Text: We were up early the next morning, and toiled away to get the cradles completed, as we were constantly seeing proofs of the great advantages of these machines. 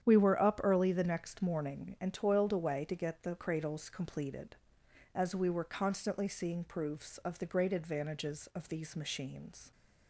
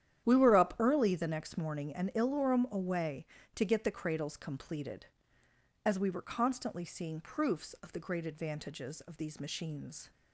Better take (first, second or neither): first